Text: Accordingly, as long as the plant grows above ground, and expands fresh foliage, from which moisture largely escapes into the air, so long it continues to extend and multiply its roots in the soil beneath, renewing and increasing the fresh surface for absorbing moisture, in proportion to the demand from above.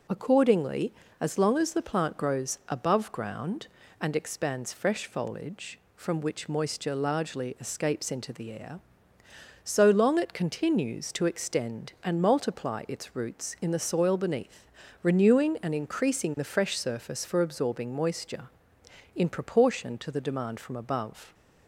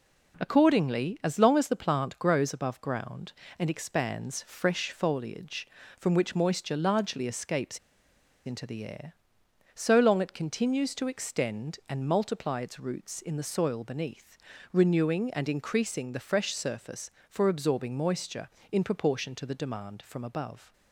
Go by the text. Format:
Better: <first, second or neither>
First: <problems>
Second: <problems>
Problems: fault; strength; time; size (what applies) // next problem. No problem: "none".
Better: first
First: none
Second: pauses between "escapes" and "into"; noticeable; at 7.7 s; 0.67 s long